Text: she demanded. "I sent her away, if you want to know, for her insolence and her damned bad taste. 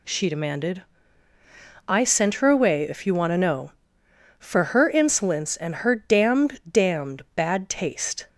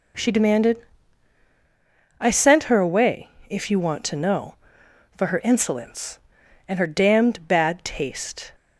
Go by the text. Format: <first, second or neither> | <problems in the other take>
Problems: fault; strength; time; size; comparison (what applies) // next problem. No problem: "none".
second | says "damned" twice; at 6.7 s